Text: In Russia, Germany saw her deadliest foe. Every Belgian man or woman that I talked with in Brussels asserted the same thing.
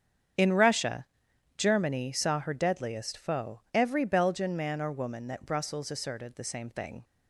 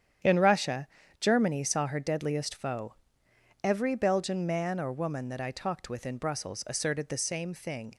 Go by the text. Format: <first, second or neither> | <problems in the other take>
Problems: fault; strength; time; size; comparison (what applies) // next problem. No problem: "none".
second | starts louder than the rest; strong; until 1.9 s; 8 dB; strong in the second // skips "I talked with in"; at 5.4 s